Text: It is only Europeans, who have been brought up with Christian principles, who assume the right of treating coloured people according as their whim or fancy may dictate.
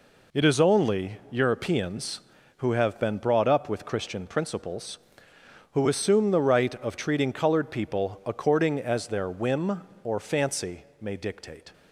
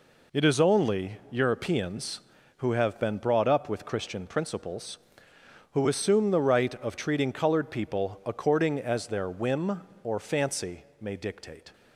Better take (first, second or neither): neither